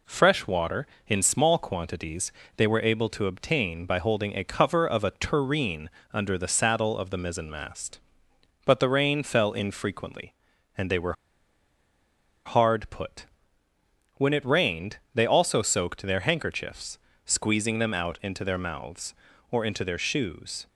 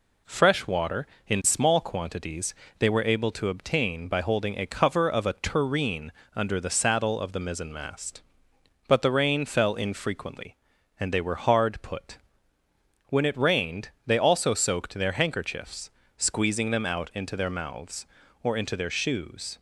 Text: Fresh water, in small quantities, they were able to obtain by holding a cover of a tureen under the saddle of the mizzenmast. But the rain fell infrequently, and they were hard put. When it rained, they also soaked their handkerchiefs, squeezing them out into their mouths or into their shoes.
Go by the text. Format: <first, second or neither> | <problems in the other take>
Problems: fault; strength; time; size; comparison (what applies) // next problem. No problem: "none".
second | pauses between "tureen" and "under"; slight; at 5.8 s; 0.24 s long; slight in the second // pauses between "were" and "hard"; strong; at 11.1 s; 1.3 s long